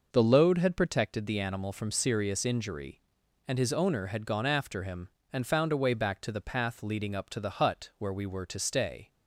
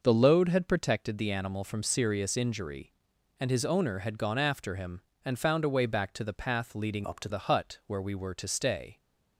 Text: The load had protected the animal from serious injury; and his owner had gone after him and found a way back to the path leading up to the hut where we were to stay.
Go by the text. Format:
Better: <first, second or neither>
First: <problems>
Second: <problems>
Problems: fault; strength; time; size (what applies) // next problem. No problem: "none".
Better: first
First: none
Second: changes voice from "up" to "to"; from 7.0 to 7.2 s; 0.2 s long